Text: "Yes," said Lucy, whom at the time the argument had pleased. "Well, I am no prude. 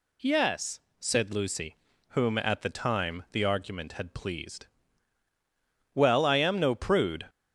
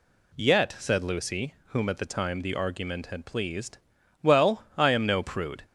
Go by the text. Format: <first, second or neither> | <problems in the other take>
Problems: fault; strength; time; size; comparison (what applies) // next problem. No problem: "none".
first | says "Yet" for "Yes"; at 0.3 s